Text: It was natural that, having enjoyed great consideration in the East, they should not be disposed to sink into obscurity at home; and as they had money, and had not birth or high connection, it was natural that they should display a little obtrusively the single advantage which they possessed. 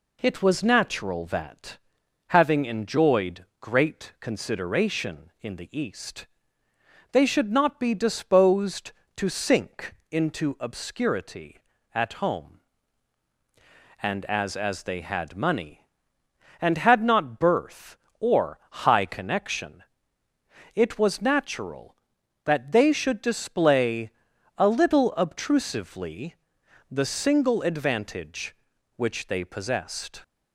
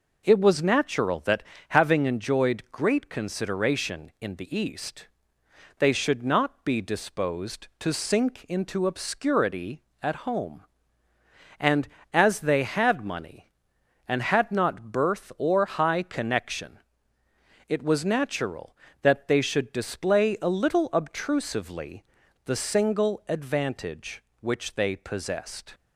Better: second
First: pauses between "enjoyed" and "great"; slight; at 3.4 s; 0.16 s long // pauses between "sink" and "into"; slight; at 9.9 s; 0.16 s long // says "as" twice; at 14.5 s // pauses between "display" and "a"; noticeable; at 24.1 s; 0.46 s long // pauses between "obtrusively" and "the"; noticeable; at 26.3 s; 0.56 s long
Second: pauses between "obtrusively" and "the"; at 22.0 s; 0.44 s long

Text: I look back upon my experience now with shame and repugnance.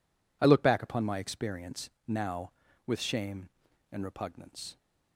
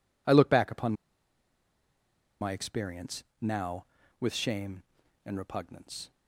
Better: first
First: pauses between "experience" and "now"; slight; at 1.9 s; 0.16 s long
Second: pauses between "upon" and "my"; strong; at 0.9 s; 1.4 s long // pauses between "experience" and "now"; slight; at 3.2 s; 0.16 s long

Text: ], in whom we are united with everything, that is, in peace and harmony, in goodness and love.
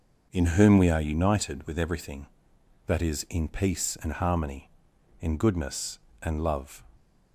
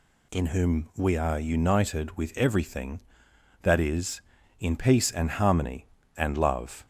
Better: first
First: none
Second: skips "in goodness"; at 6.0 s

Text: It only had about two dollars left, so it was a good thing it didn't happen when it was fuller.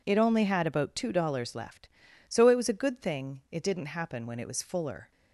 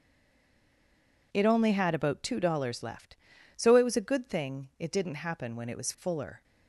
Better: first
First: none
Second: stays silent before the first word; noticeable; until 1.3 s; 1.3 s long

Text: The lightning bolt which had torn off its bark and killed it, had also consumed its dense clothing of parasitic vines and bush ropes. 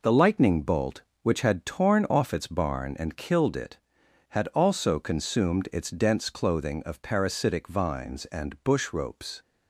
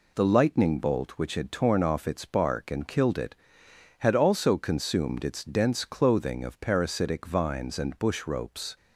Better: second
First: says "barn" for "bark"; at 2.4 s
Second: none

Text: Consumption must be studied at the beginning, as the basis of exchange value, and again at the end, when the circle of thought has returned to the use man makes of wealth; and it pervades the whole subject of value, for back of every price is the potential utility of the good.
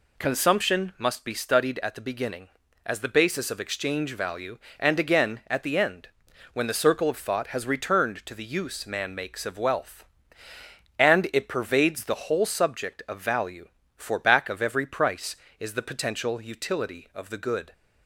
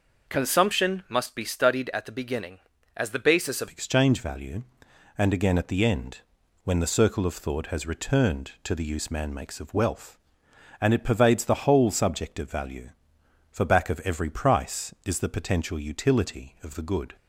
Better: first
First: none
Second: changes voice at "exchange"; from 3.6 s on; 13.5 s long

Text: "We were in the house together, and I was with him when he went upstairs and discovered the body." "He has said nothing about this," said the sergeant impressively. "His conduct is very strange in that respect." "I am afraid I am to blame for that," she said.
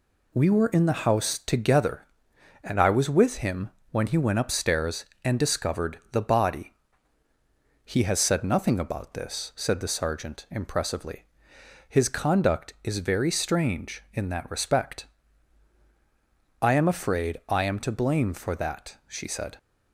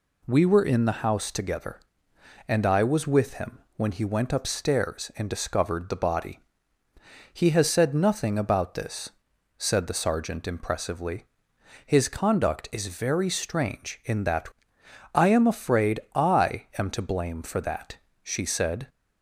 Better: first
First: pauses between "him" and "when"; slight; at 3.6 s; 0.22 s long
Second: pauses between "him" and "when"; slight; at 3.5 s; 0.16 s long // skips "respect"; at 14.8 s

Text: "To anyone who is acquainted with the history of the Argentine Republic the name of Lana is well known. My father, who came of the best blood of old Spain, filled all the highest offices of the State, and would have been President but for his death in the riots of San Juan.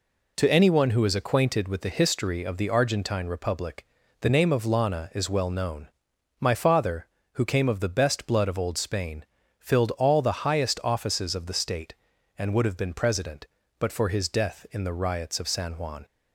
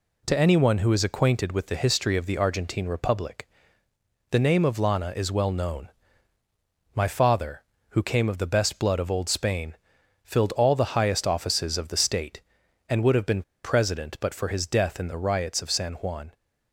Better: first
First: pauses between "Republic" and "the"; slight; at 3.8 s; 0.36 s long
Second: pauses between "Republic" and "the"; noticeable; at 3.4 s; 0.84 s long // pauses between "been" and "President"; slight; at 13.4 s; 0.21 s long

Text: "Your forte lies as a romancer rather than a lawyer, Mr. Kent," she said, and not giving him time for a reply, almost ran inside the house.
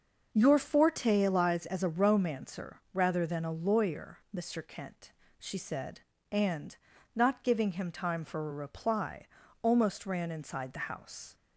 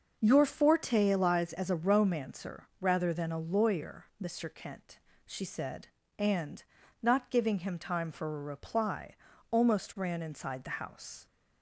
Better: neither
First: pauses between "and" and "not"; at 6.7 s; 0.40 s long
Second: pauses between "and" and "not"; at 6.6 s; 0.40 s long

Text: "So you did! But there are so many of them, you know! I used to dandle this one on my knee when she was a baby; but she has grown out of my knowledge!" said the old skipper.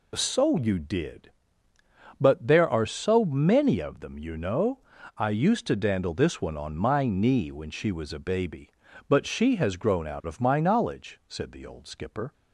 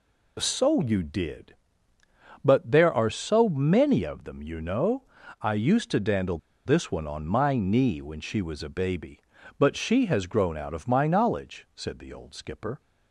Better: first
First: none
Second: pauses between "dandle" and "this"; slight; at 6.3 s; 0.27 s long

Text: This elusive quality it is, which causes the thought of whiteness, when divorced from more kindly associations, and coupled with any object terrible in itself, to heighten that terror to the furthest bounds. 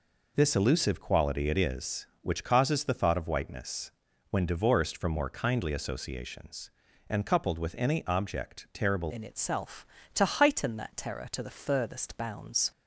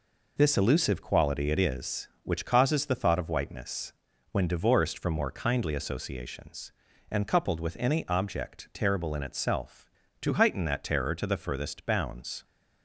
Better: second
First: changes voice at "in"; from 9.1 s on; 3.6 s long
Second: none

